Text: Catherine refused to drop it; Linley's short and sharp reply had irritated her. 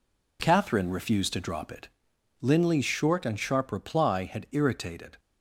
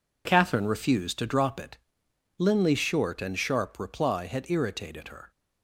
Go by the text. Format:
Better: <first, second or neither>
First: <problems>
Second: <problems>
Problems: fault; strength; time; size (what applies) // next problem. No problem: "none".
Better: second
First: stops before "her"; at 5.1 s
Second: none